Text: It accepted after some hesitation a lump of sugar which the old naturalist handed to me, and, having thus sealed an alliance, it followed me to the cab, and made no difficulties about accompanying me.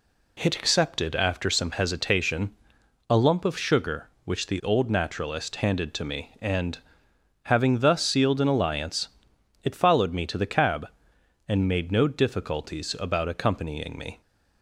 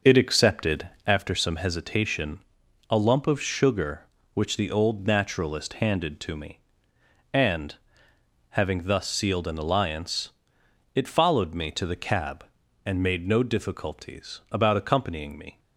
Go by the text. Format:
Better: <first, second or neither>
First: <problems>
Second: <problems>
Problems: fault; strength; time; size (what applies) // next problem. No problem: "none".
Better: first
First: pauses between "hesitation" and "a"; noticeable; at 2.5 s; 0.58 s long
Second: starts louder than the rest; noticeable; until 1.3 s; 6 dB // pauses between "accepted" and "after"; slight; at 0.8 s; 0.18 s long // pauses between "hesitation" and "a"; noticeable; at 2.3 s; 0.50 s long